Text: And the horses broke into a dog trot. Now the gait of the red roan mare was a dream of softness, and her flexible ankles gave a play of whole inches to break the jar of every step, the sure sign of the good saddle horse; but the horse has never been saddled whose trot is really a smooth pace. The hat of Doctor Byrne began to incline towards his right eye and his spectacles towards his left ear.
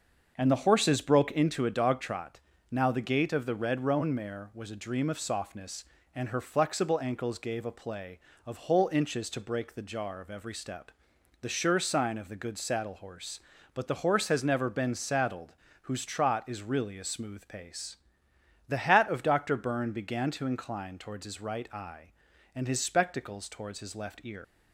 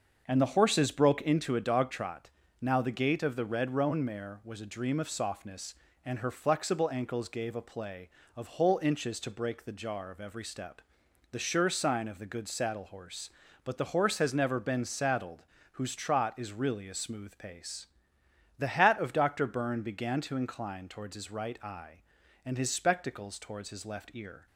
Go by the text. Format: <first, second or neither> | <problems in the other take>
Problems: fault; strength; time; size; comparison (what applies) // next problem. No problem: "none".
second | starts louder than the rest; until 1.3 s; 6.5 dB; also in the second // pauses between "saddled" and "whose"; slight; at 15.5 s; 0.30 s long; slight in the second // leaves "ear" unfinished; at 24.4 s; 115 ms